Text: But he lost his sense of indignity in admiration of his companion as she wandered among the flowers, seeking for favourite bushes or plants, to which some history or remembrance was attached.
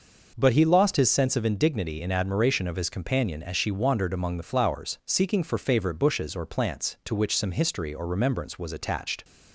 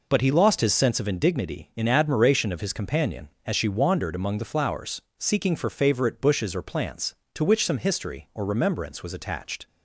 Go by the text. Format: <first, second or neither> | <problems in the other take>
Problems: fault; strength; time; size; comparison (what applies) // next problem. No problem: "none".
neither | none